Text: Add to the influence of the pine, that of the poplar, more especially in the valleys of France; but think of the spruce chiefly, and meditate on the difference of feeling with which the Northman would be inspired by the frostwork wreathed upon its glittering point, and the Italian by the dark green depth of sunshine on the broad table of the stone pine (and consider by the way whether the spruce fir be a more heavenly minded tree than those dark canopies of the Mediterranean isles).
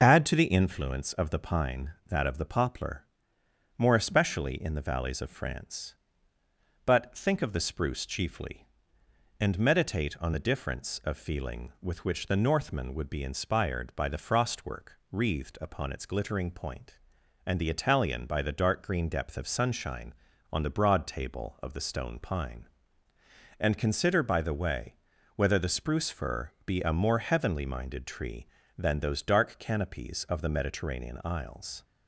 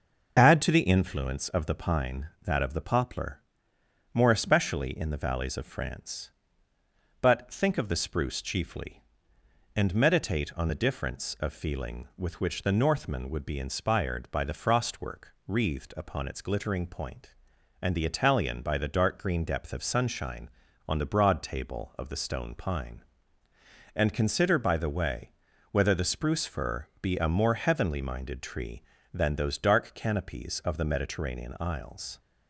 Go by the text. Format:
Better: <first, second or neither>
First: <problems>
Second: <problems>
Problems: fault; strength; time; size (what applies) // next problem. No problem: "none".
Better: neither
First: pauses between "frostwork" and "wreathed"; slight; at 14.9 s; 0.16 s long // pauses between "way" and "whether"; at 24.9 s; 0.42 s long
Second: pauses between "frostwork" and "wreathed"; slight; at 15.3 s; 0.16 s long // pauses between "way" and "whether"; at 25.2 s; 0.42 s long